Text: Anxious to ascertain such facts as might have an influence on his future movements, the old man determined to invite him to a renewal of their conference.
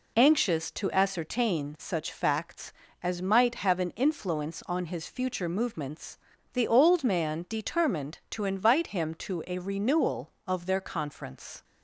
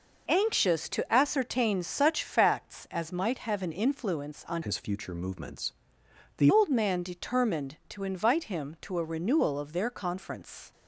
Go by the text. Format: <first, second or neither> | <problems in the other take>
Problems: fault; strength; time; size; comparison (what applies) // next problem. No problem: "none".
first | changes voice from "his" to "the"; from 4.6 to 6.5 s; 1.9 s long